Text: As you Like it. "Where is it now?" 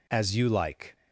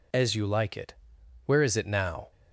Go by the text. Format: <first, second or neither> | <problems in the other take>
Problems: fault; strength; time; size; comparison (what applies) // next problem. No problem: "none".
second | stops before "it Where is it now"; at 0.9 s